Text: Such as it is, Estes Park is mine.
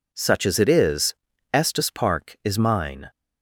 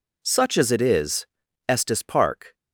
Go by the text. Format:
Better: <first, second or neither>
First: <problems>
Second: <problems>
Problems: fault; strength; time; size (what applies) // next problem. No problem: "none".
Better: first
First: none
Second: stops before "is mine"; at 2.5 s